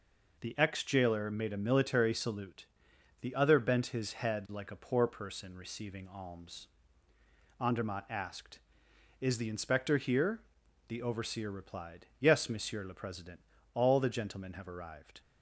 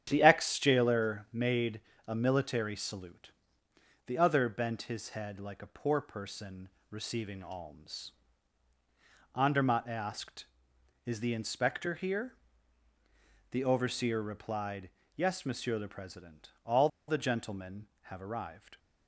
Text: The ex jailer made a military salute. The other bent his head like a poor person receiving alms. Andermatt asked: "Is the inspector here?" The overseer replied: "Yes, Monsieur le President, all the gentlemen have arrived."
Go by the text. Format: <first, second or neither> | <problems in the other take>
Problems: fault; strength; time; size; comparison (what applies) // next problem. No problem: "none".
first | starts louder than the rest; strong; until 1.0 s; 9 dB // pauses between "made" and "a"; slight; at 1.8 s; 0.26 s long // pauses between "person" and "receiving"; slight; at 6.6 s; 0.22 s long // pauses between "all" and "the"; slight; at 16.8 s; 0.19 s long